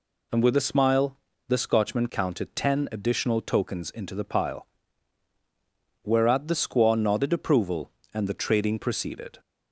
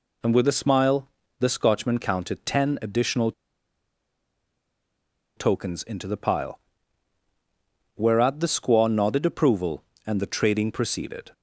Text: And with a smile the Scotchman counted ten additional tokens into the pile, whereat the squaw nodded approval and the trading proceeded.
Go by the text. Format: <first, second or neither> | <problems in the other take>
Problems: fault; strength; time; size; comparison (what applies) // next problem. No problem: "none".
first | pauses between "smile" and "the"; slight; at 1.0 s; 0.32 s long; slight in the first // pauses between "additional" and "tokens"; strong; at 3.3 s; 2.0 s long